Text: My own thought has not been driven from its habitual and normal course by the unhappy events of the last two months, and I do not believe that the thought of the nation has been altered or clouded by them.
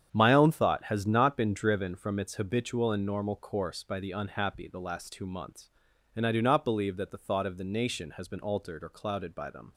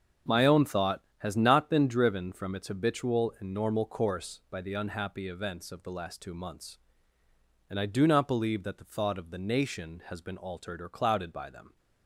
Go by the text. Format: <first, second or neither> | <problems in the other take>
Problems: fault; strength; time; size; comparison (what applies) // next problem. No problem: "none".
second | starts louder than the rest; strong; until 1.1 s; 8.5 dB; also in the second // skips "events of"; at 4.6 s